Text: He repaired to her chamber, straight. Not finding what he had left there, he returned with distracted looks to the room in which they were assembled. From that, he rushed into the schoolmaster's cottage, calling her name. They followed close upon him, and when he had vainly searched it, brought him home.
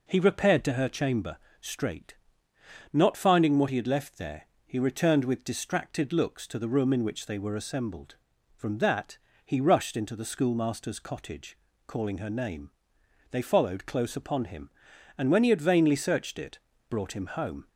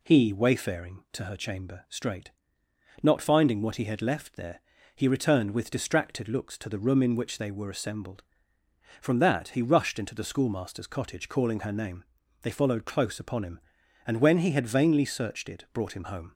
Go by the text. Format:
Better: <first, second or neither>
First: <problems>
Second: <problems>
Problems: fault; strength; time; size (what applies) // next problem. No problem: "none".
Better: first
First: none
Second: says "wayfaring" for "repaired"; at 0.3 s